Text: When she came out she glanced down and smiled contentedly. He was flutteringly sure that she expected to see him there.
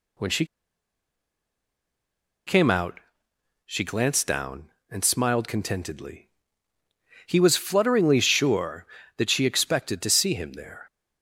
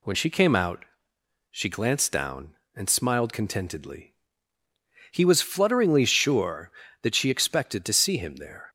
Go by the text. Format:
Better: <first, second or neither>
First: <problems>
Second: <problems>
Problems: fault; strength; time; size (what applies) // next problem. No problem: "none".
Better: second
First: pauses between "she" and "came"; strong; at 0.4 s; 2.0 s long // pauses between "out" and "she"; noticeable; at 2.9 s; 0.66 s long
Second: pauses between "out" and "she"; noticeable; at 0.8 s; 0.66 s long